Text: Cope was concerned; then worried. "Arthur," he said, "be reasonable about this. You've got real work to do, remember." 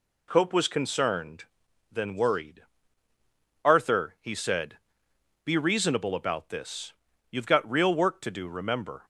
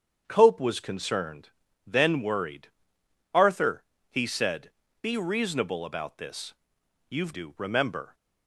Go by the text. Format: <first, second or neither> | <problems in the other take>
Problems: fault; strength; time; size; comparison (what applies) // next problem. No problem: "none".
first | starts louder than the rest; strong; until 1.2 s; 8 dB // skips "got real work to"; at 7.3 s